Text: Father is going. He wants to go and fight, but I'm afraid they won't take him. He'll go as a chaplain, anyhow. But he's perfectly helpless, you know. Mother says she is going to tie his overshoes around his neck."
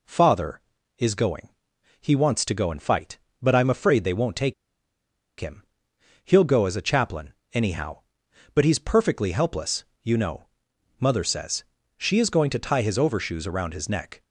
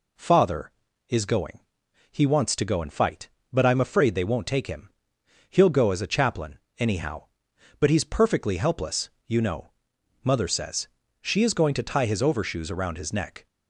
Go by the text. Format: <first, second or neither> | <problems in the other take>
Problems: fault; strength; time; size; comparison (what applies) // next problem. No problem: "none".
second | pauses between "take" and "him"; noticeable; at 4.5 s; 0.86 s long // pauses between "says" and "she"; slight; at 11.6 s; 0.32 s long; slight in the second